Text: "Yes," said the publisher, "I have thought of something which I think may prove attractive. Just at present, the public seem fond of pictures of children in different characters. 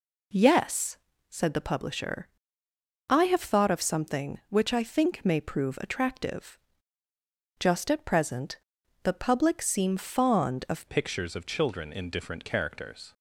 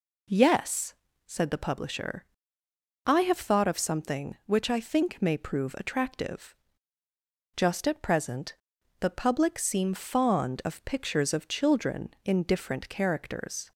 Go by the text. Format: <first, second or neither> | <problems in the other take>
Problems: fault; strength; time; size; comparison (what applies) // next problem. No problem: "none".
second | changes voice at "pictures"; from 10.8 s on; 2.3 s long